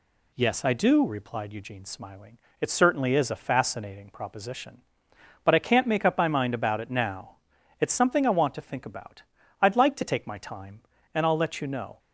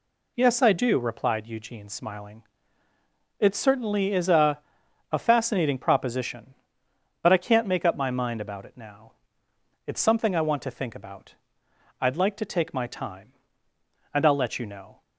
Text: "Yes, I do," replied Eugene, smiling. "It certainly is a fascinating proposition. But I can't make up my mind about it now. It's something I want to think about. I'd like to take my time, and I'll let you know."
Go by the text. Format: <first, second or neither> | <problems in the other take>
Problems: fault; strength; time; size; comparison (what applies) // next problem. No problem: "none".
first | says "a" twice; at 5.1 s